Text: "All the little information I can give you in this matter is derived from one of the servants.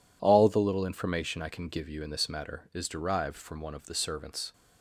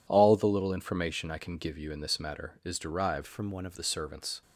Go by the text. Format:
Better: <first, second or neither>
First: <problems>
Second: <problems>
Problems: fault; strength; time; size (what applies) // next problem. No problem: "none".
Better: first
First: none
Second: changes voice from "from" to "of"; from 3.2 to 3.7 s; 0.5 s long